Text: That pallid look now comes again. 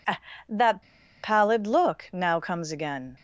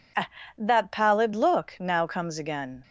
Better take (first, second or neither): second